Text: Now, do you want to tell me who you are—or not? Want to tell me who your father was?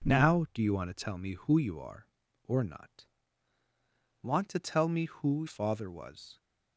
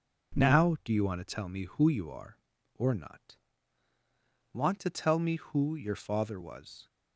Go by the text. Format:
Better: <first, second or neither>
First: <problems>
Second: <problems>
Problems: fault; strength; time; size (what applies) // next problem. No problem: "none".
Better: second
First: skips "your"; at 5.4 s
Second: none